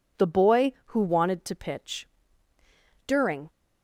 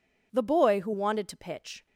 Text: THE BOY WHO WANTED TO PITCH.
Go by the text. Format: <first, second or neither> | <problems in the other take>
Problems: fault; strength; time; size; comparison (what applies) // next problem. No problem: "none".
second | goes on to say "During"; slight; from 3.0 s on; 0.42 s long